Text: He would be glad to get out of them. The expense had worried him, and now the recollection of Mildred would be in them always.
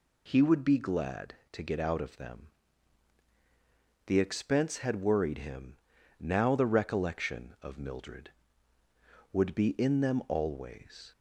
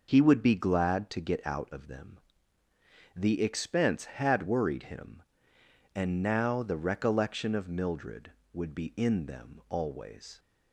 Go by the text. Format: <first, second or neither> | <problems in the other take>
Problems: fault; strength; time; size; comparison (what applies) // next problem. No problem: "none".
second | skips "and"; at 5.9 s